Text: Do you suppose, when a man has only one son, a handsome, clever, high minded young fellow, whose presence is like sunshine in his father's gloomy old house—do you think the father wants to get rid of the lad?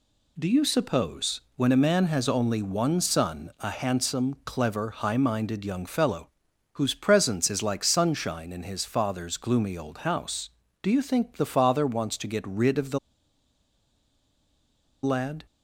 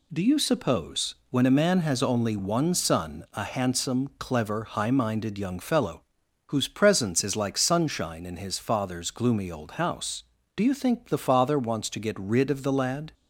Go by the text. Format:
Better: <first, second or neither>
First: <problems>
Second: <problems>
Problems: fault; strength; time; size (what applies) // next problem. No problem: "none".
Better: second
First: pauses between "the" and "lad"; strong; at 12.9 s; 2.0 s long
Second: none